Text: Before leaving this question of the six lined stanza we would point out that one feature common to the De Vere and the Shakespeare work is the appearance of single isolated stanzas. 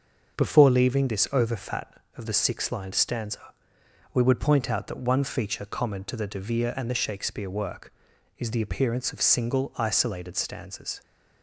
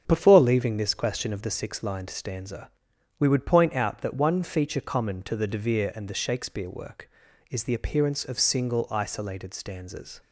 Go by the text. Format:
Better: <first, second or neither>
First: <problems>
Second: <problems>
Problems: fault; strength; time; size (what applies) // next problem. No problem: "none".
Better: second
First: starts louder than the rest; until 1.4 s; 6.5 dB // says "overfat" for "question"; at 1.3 s // pauses between "stanza" and "we"; noticeable; at 3.5 s; 0.60 s long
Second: starts louder than the rest; until 1.0 s; 7 dB // pauses between "stanza" and "we"; noticeable; at 2.7 s; 0.48 s long